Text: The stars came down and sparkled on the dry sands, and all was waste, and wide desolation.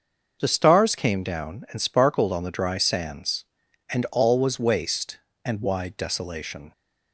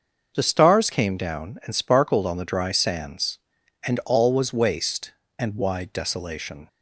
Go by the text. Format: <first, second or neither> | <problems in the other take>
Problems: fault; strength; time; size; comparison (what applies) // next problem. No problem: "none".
neither | starts louder than the rest; noticeable; the same in both